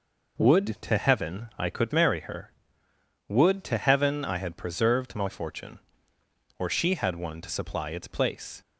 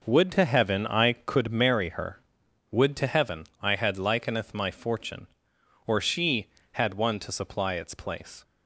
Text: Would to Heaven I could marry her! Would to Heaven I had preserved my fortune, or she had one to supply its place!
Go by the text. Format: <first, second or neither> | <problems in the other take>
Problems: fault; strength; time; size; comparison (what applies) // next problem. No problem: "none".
first | says "likeneth" for "preserved"; at 3.9 s